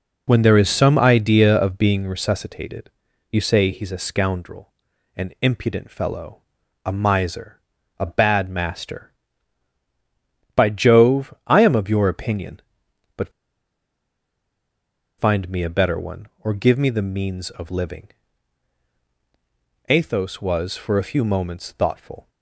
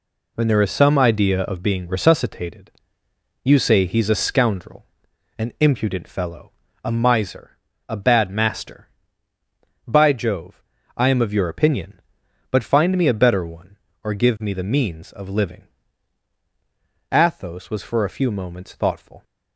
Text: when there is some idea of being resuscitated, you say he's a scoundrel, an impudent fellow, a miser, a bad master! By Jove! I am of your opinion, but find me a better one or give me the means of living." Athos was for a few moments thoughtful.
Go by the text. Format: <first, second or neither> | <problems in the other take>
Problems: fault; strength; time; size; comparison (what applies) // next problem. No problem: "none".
second | pauses between "but" and "find"; strong; at 13.3 s; 1.8 s long